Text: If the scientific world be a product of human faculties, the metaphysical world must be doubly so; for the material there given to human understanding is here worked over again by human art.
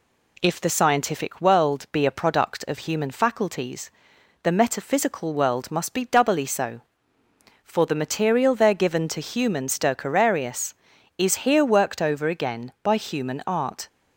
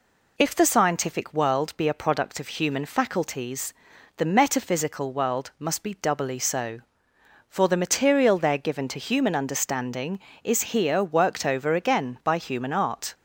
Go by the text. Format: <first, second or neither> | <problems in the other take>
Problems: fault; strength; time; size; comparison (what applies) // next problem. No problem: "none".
second | says "stercorarius" for "understanding"; at 9.6 s